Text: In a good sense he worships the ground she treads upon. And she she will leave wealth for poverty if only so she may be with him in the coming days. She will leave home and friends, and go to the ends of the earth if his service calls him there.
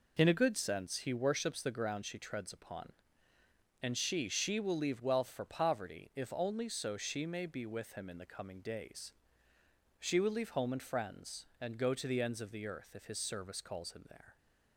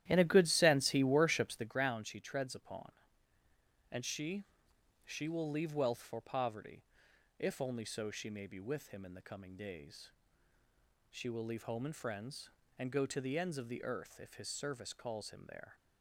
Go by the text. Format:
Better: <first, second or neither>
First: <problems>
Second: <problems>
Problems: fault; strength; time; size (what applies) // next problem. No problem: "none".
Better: first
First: none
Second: starts louder than the rest; strong; until 1.8 s; 12.5 dB // pauses between "she" and "she"; noticeable; at 4.4 s; 0.60 s long // pauses between "poverty" and "if"; noticeable; at 6.8 s; 0.56 s long